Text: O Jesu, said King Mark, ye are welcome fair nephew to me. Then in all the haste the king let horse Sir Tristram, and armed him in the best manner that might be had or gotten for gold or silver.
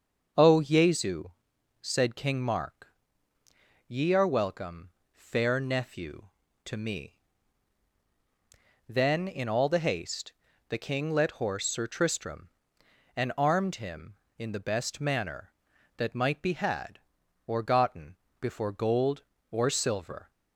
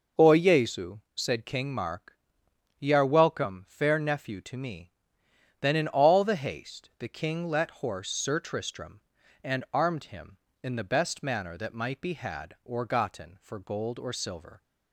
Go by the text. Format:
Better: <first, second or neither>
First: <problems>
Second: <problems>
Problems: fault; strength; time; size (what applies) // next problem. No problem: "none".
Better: second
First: starts louder than the rest; until 1.8 s; 6.5 dB // pauses between "welcome" and "fair"; slight; at 4.8 s; 0.24 s long // pauses between "haste" and "the"; slight; at 10.3 s; 0.34 s long // says "before" for "for"; at 18.4 s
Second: none